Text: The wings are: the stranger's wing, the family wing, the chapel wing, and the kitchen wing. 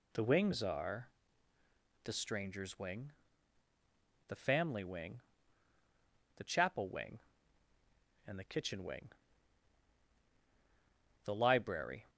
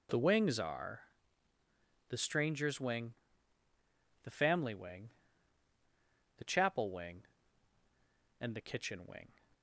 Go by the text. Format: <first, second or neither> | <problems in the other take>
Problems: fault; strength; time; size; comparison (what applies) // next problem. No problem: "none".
second | goes on to say "The library"; noticeable; from 11.2 s on; 0.84 s long